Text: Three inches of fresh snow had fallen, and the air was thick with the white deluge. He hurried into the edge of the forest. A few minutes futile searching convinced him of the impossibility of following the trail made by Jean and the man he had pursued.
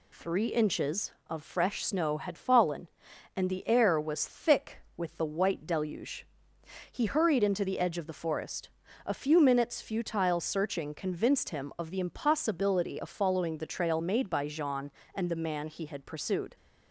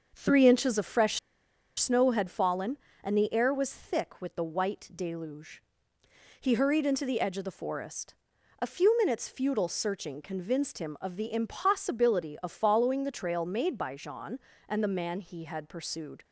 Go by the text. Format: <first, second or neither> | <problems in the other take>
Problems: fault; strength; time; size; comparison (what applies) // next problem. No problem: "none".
first | starts louder than the rest; until 1.1 s; 6.5 dB // pauses between "fresh" and "snow"; noticeable; at 1.1 s; 0.60 s long